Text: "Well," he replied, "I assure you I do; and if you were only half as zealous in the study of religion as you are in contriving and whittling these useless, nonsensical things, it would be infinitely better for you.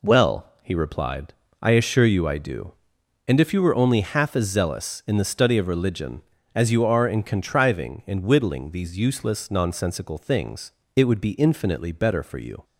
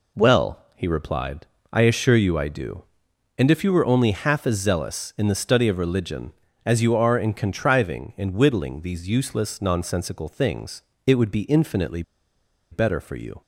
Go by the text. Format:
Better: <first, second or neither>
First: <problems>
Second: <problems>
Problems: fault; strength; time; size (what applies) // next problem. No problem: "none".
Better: first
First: none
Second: pauses between "infinitely" and "better"; noticeable; at 12.0 s; 0.69 s long